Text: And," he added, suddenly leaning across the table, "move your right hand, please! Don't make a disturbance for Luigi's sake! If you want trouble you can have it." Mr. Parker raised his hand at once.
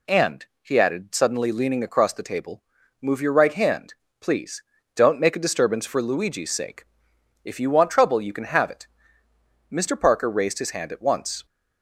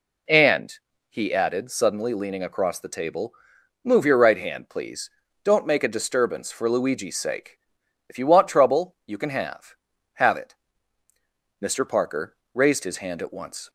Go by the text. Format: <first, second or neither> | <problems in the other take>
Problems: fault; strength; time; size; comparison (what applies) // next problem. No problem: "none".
first | says "have" twice; at 10.1 s // pauses between "Parker" and "raised"; slight; at 12.3 s; 0.20 s long